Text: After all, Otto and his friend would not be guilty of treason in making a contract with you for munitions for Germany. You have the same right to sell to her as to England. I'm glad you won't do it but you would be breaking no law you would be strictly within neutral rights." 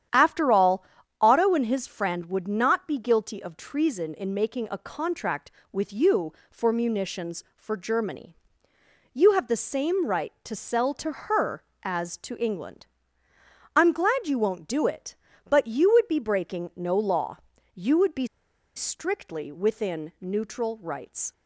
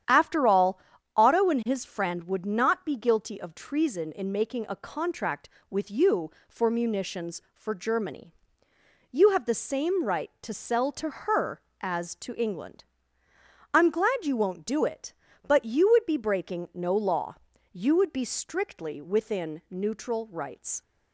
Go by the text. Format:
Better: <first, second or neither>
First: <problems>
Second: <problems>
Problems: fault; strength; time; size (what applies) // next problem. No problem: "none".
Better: second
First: starts louder than the rest; strong; until 1.5 s; 10 dB // pauses between "law" and "you"; slight; at 17.3 s; 0.36 s long // pauses between "be" and "strictly"; noticeable; at 18.2 s; 0.48 s long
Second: starts louder than the rest; strong; until 1.4 s; 10 dB // pauses between "law" and "you"; slight; at 17.3 s; 0.36 s long